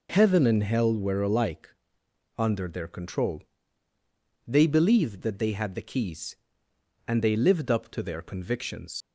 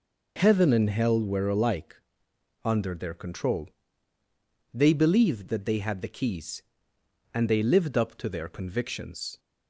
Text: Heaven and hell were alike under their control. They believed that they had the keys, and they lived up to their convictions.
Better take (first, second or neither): second